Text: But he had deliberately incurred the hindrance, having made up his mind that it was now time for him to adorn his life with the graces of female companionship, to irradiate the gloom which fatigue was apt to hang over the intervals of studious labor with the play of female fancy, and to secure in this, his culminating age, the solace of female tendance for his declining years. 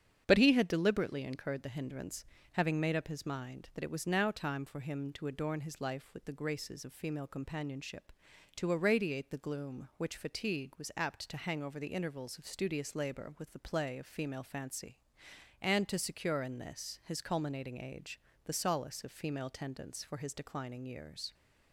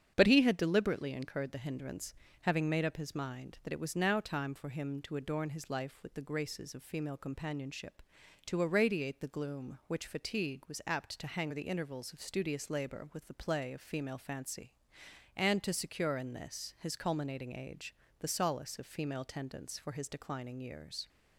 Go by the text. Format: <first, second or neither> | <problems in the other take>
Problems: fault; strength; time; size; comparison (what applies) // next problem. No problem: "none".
first | starts louder than the rest; strong; until 1.1 s; 8 dB; strong in the first // skips "over"; at 11.5 s